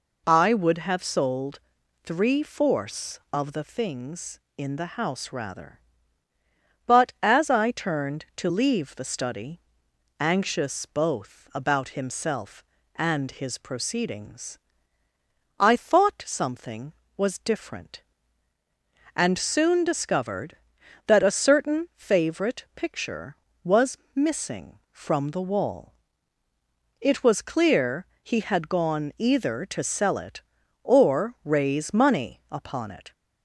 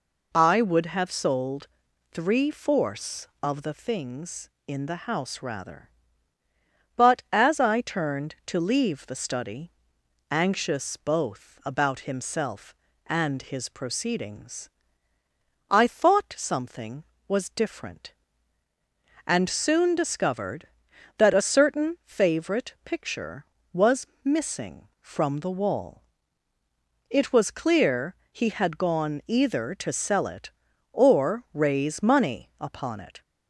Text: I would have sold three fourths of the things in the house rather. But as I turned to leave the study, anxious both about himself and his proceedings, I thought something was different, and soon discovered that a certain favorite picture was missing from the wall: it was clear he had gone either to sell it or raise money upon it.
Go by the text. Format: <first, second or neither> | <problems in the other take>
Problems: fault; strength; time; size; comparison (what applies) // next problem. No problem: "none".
neither | pauses between "sold" and "three"; the same in both // pauses between "was" and "missing"; slight; the same in both // pauses between "clear" and "he"; slight; the same in both